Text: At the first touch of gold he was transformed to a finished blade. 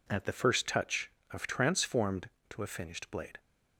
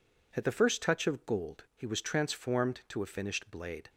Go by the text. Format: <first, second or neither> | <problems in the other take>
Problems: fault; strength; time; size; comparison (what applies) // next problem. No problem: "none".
second | skips "gold he was"; at 1.4 s